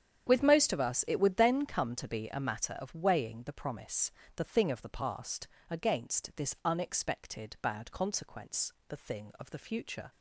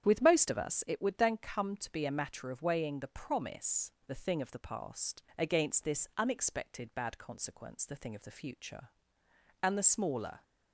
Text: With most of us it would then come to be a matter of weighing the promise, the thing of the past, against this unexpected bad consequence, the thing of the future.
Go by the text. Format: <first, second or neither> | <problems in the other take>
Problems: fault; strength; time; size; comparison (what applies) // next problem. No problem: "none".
first | starts louder than the rest; strong; until 1.0 s; 9 dB; strong in the first // goes on to say "And the smaller"; noticeable; from 9.6 s on; 0.80 s long